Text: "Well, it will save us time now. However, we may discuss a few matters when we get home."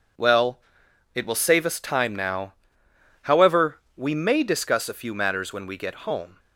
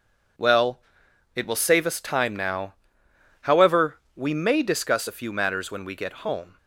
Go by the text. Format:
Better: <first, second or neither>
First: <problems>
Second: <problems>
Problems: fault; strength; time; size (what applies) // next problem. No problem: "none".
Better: neither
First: none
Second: none